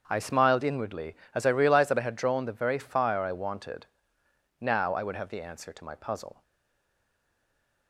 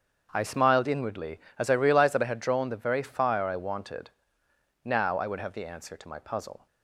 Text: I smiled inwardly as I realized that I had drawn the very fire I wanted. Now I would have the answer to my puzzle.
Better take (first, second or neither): second